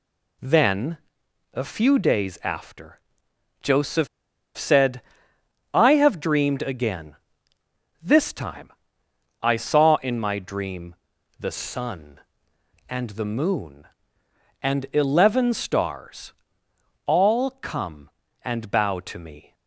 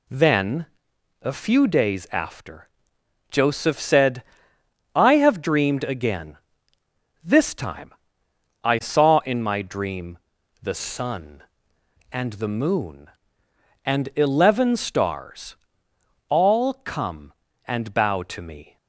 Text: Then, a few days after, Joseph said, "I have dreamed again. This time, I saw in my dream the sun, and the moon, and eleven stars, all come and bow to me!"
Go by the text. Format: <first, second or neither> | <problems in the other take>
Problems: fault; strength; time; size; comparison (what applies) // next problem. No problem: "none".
second | pauses between "Joseph" and "said"; noticeable; at 4.0 s; 0.49 s long // pauses between "dream" and "the"; noticeable; at 10.9 s; 0.46 s long; noticeable in the second